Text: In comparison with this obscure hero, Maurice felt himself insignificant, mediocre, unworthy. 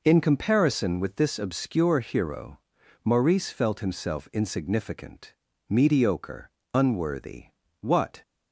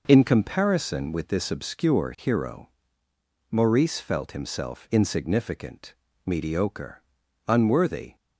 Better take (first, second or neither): second